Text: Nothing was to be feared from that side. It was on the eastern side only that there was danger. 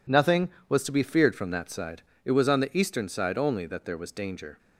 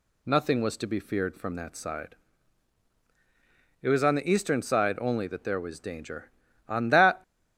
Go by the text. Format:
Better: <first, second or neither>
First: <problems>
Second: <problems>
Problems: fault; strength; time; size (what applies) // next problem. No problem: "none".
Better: first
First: none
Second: goes on to say "On that"; from 6.6 s on; 0.54 s long